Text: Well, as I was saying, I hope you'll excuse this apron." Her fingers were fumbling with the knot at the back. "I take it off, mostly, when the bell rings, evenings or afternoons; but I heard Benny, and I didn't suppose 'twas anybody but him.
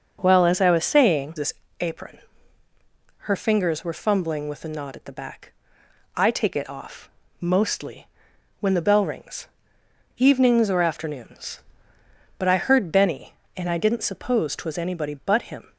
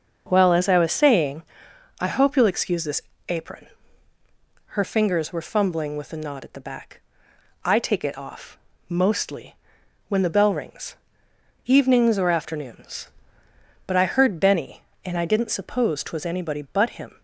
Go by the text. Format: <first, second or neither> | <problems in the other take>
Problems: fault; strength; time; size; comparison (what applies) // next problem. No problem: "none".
second | starts louder than the rest; until 1.2 s; 6 dB; also in the second // skips "I hope you'll excuse"; at 1.3 s // pauses between "this" and "apron"; slight; at 1.5 s; 0.28 s long; slight in the second